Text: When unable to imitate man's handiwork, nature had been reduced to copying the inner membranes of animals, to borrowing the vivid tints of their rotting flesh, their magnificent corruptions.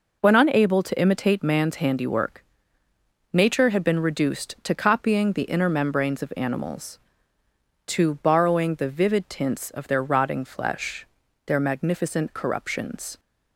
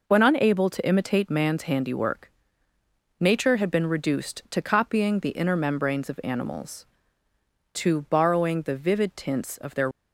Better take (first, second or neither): first